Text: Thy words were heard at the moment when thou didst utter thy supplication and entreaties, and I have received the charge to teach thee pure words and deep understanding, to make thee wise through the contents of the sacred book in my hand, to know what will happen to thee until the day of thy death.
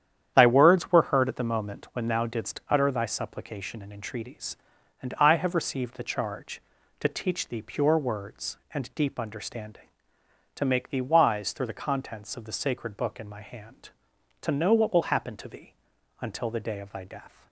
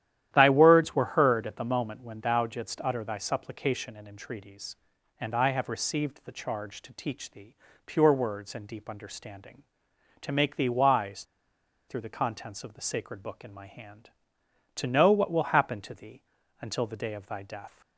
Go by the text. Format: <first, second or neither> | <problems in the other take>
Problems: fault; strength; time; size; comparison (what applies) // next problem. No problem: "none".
first | starts louder than the rest; strong; until 1.3 s; 12 dB; strong in the first // pauses between "thee" and "pure"; slight; at 7.5 s; 0.30 s long // pauses between "wise" and "through"; noticeable; at 11.2 s; 0.63 s long // pauses between "thee" and "until"; at 16.2 s; 0.38 s long; also in the first